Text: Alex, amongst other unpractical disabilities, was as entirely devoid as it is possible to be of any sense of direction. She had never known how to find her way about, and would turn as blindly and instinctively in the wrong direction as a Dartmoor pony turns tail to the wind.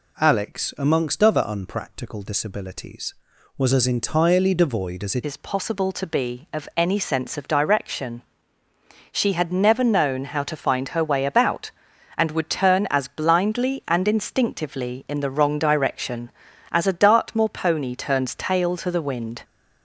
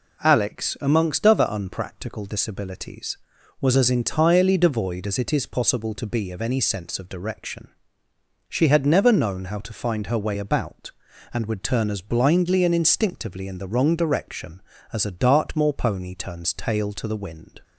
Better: second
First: changes voice at "is"; from 5.2 s on; 14.2 s long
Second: none

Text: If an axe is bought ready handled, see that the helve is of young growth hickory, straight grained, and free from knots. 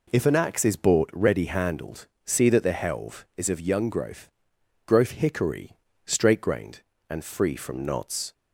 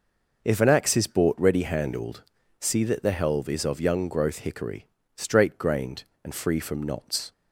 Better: second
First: says "growth" twice; at 4.8 s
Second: none

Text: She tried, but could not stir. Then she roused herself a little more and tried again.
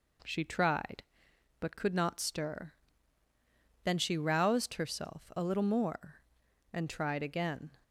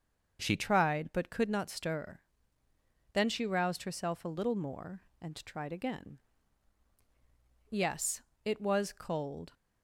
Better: first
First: none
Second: starts louder than the rest; until 1.4 s; 6.5 dB // goes on to say "Yes it was cold"; strong; from 7.7 s on; 1.8 s long

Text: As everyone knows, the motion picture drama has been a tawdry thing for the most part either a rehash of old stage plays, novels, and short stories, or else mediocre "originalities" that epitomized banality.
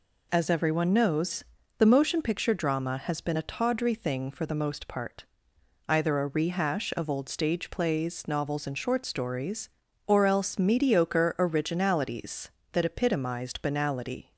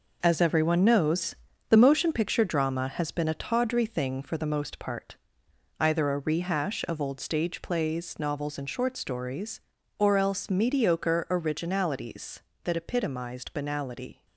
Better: first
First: pauses between "part" and "either"; noticeable; at 5.2 s; 0.66 s long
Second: gets quieter; strong; throughout; 8 dB // pauses between "part" and "either"; noticeable; at 5.1 s; 0.66 s long

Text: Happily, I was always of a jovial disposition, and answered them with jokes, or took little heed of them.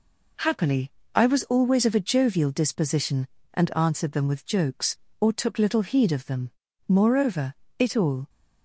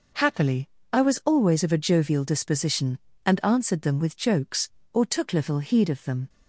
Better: second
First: goes on to say "Moreover it all"; from 6.8 s on; 1.4 s long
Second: none

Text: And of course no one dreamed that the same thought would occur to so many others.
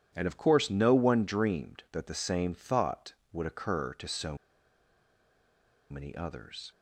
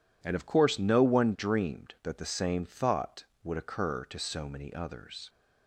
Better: second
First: pauses between "so" and "many"; strong; at 4.3 s; 1.5 s long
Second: none

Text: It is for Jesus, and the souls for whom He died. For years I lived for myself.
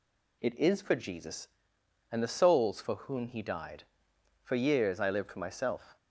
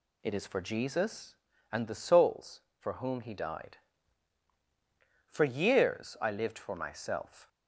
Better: neither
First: none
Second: none

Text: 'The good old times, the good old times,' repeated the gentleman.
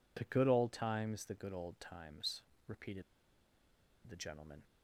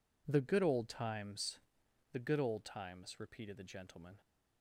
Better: second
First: pauses between "repeated" and "the"; at 3.0 s; 1.0 s long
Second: none

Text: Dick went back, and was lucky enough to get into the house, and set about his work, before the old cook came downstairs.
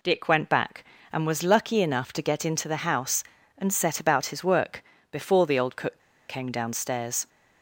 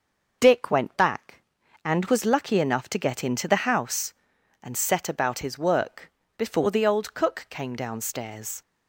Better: second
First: pauses between "cook" and "came"; slight; at 6.0 s; 0.27 s long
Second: none

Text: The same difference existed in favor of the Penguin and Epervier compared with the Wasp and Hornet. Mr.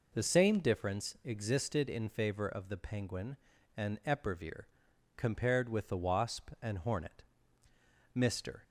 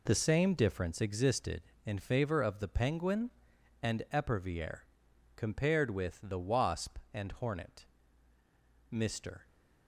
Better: first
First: pauses between "Epervier" and "compared"; noticeable; at 4.6 s; 0.52 s long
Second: gets quieter; strong; throughout; 10.5 dB // pauses between "Epervier" and "compared"; noticeable; at 4.8 s; 0.52 s long

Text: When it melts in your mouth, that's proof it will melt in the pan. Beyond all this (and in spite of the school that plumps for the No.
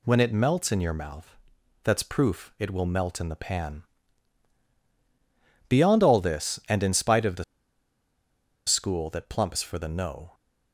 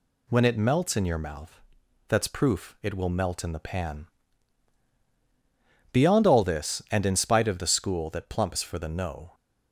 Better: second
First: pauses between "the" and "school"; at 7.4 s; 1.2 s long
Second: none

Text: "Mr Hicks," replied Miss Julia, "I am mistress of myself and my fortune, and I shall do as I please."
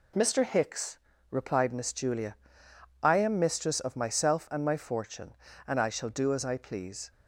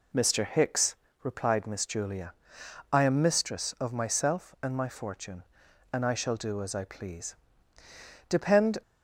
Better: first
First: none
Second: goes on to say "Depend"; from 8.2 s on; 0.54 s long

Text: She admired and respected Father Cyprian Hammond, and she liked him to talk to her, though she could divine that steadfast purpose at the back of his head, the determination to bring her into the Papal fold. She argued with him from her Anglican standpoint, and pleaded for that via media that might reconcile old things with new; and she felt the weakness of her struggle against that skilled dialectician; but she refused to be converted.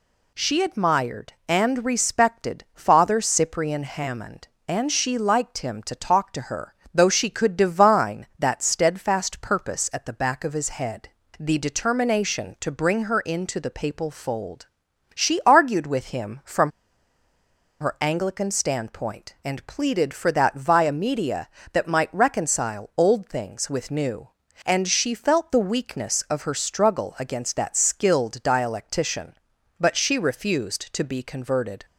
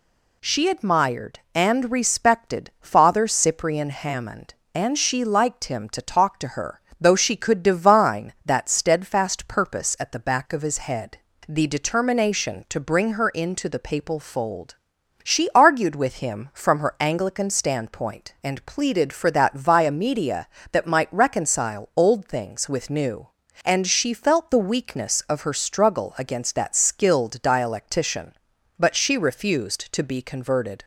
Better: second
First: pauses between "from" and "her"; at 16.7 s; 1.1 s long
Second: none

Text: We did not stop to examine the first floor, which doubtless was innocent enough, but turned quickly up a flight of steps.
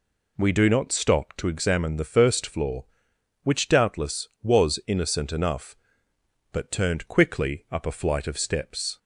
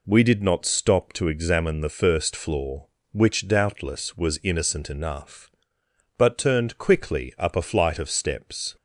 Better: second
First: says "do" for "did"; at 0.5 s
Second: none

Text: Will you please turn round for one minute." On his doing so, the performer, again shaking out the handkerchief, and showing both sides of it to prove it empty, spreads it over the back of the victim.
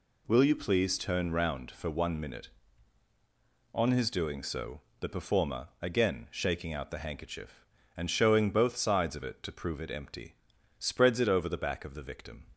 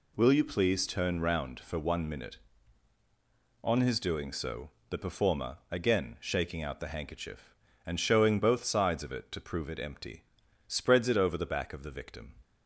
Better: neither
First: none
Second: none

